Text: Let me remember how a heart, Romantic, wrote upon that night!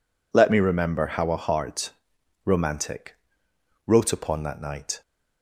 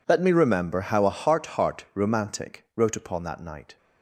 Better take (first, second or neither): first